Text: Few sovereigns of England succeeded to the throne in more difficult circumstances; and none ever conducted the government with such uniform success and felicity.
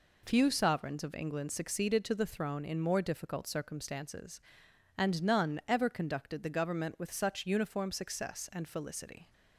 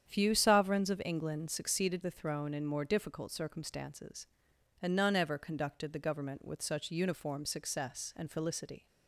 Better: first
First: none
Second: starts louder than the rest; strong; until 1.1 s; 8.5 dB // skips "to"; at 2.0 s

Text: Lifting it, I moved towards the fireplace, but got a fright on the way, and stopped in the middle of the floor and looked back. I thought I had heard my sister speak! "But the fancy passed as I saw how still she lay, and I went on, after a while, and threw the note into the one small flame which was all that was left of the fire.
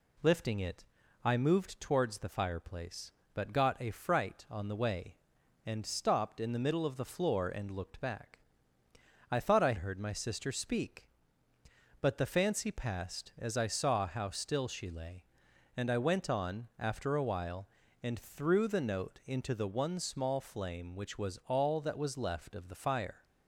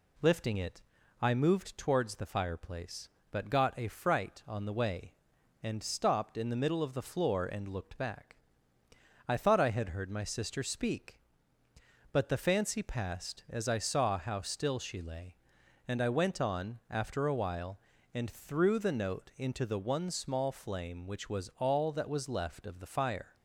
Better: second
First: skips "had"; at 9.7 s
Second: none

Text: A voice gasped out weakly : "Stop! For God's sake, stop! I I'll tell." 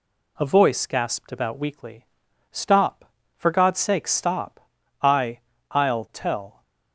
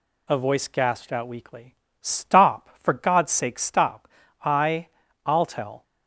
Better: second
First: says "about" for "out"; at 1.3 s // pauses between "I" and "I'll"; slight; at 5.3 s; 0.32 s long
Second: pauses between "I" and "I'll"; at 4.8 s; 0.38 s long

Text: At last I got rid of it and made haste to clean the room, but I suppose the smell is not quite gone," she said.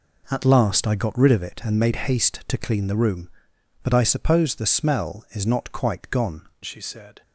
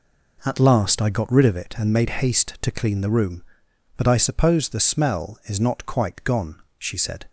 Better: second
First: changes voice at "she"; from 6.6 s on; 0.6 s long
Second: none

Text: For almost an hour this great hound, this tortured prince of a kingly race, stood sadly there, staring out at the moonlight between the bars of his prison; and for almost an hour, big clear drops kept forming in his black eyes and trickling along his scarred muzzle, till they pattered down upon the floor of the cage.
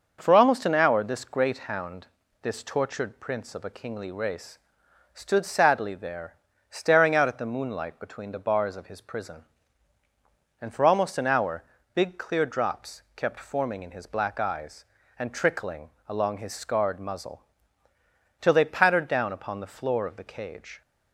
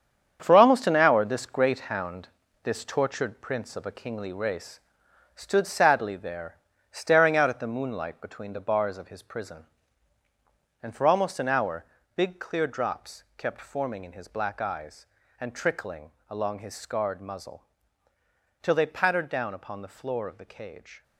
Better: first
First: starts louder than the rest; noticeable; until 1.2 s; 6 dB // pauses between "trickling" and "along"; slight; at 15.8 s; 0.16 s long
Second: gets quieter; strong; throughout; 8.5 dB // starts louder than the rest; strong; until 1.4 s; 8 dB // pauses between "trickling" and "along"; slight; at 16.1 s; 0.16 s long

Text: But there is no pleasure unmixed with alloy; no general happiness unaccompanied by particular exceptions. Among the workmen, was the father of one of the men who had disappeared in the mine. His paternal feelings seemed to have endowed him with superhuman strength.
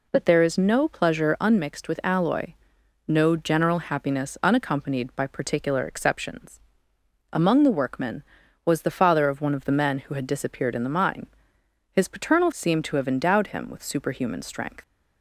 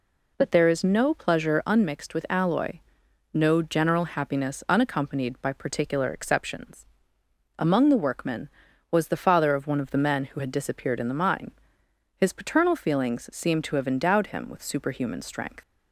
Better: second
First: skips "feelings"; at 12.5 s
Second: none

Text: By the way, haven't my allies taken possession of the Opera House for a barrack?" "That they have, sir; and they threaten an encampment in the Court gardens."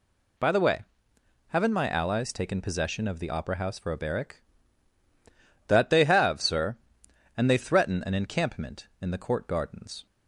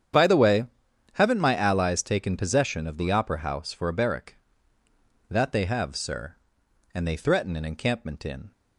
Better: first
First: none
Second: starts louder than the rest; strong; until 1.6 s; 8.5 dB // stops before "the Court gardens"; at 8.5 s

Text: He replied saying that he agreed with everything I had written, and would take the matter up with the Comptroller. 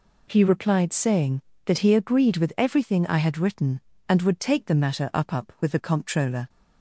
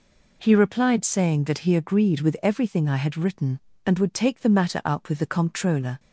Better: second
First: says "up" twice; at 5.3 s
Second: none

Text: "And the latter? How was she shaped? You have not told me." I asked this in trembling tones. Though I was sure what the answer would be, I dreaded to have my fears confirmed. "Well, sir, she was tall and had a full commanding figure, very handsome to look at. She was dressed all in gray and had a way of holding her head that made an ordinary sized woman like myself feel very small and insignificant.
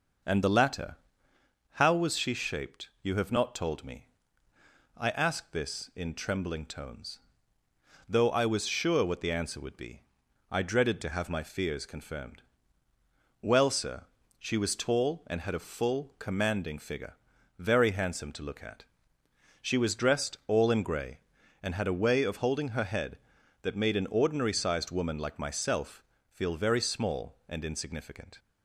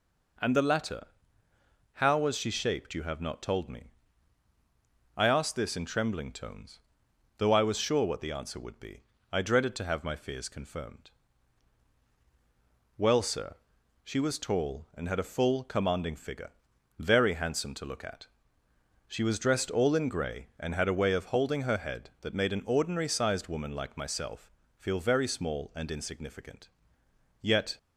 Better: first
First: pauses between "myself" and "feel"; slight; at 26.0 s; 0.28 s long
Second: pauses between "myself" and "feel"; slight; at 24.5 s; 0.28 s long // goes on to say "Yet"; slight; from 27.3 s on; 0.38 s long

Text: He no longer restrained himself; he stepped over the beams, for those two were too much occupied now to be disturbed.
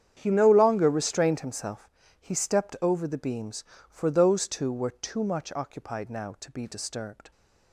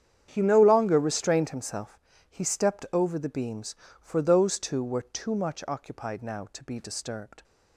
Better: neither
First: starts louder than the rest; strong; until 1.2 s; 9 dB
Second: starts louder than the rest; strong; until 1.3 s; 9 dB

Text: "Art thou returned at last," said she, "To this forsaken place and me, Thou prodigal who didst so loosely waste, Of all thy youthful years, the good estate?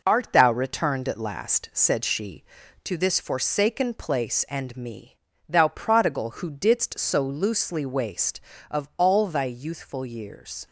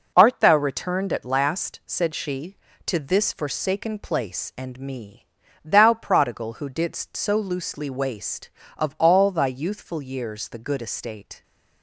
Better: second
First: stops before "the good estate"; at 10.6 s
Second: none

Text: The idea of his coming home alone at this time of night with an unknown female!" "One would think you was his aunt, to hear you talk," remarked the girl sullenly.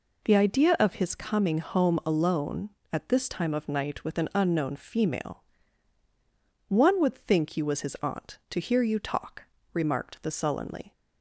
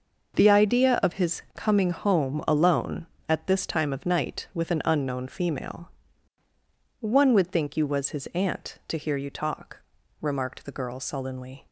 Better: second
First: skips "girl"; at 10.3 s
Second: none

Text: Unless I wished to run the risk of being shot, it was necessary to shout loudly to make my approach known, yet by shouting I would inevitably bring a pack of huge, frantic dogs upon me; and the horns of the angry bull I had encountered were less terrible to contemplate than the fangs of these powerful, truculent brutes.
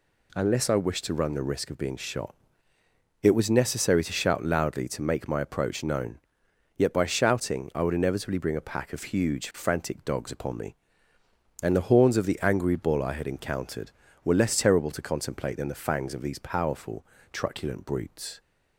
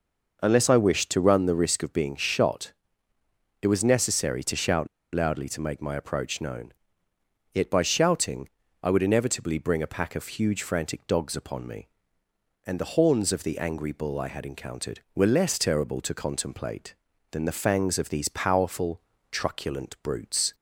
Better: first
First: none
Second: pauses between "shout" and "loudly"; slight; at 4.8 s; 0.26 s long // pauses between "shouting" and "I"; slight; at 8.4 s; 0.34 s long

